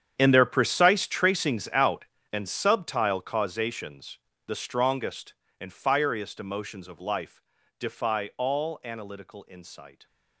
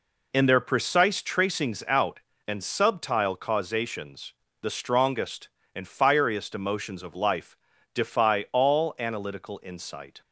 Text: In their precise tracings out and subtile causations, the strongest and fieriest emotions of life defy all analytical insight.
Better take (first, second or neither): second